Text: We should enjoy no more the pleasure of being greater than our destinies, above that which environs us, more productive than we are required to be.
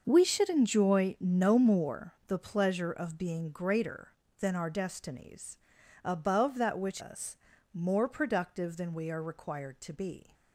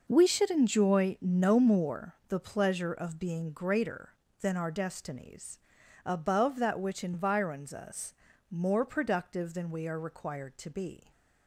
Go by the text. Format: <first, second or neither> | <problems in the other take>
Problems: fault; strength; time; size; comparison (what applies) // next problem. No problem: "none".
second | starts louder than the rest; until 1.0 s; 6 dB // skips "environs"; at 7.0 s